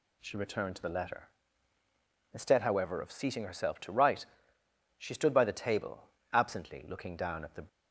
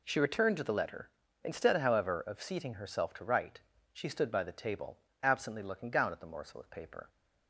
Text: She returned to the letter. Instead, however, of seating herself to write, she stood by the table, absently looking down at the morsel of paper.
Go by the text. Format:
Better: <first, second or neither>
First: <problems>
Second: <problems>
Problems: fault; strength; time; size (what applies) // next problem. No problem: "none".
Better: second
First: stops before "morsel of paper"; at 7.6 s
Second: none